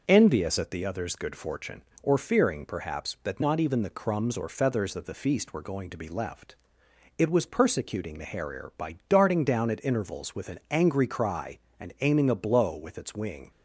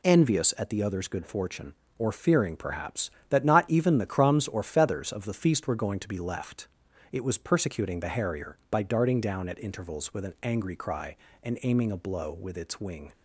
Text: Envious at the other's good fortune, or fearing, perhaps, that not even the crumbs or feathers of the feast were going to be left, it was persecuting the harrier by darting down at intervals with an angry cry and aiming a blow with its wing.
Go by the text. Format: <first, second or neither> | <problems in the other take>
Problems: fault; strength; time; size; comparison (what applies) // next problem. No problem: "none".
neither | none